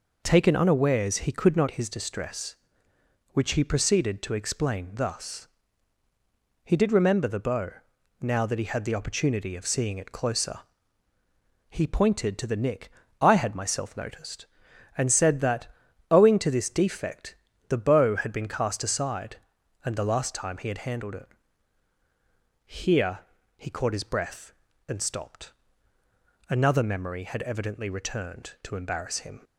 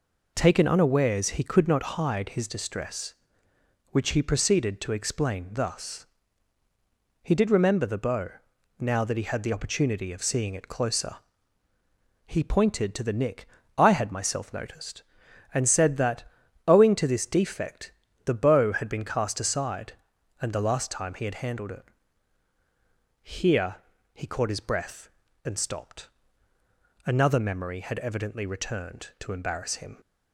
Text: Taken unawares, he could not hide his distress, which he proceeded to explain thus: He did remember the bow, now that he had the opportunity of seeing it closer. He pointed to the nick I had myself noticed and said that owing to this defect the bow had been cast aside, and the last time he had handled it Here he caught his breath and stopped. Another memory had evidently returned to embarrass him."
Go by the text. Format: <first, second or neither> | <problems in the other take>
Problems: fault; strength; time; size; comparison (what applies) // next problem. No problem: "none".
second | skips "hide"; at 1.6 s // pauses between "nick" and "I"; slight; at 12.9 s; 0.30 s long; slight in the second // pauses between "that" and "owing"; at 15.6 s; 0.42 s long; also in the second // pauses between "defect" and "the"; slight; at 17.3 s; 0.34 s long; slight in the second // pauses between "it" and "Here"; strong; at 21.2 s; 1.4 s long; strong in the second // pauses between "Here" and "he"; slight; at 23.2 s; 0.36 s long; slight in the second